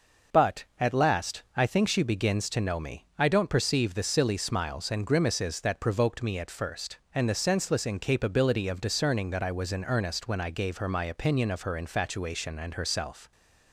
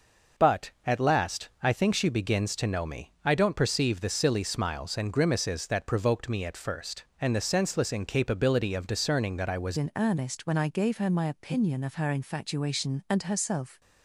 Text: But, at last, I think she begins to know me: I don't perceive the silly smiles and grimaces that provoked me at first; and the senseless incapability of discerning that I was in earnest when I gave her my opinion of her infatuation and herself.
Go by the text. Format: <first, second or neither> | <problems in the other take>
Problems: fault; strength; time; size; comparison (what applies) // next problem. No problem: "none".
first | starts louder than the rest; noticeable; until 1.6 s; 6 dB; noticeable in the first // changes voice at "in"; from 9.7 s on; 4.1 s long